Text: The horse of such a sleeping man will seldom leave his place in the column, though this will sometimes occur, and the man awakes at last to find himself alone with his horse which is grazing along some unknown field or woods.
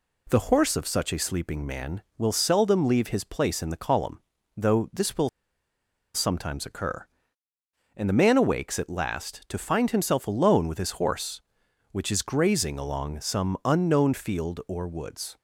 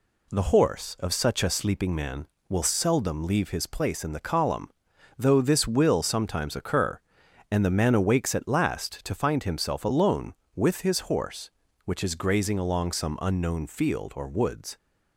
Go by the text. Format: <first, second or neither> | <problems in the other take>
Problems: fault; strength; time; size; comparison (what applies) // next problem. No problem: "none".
second | pauses between "will" and "sometimes"; noticeable; at 5.2 s; 0.85 s long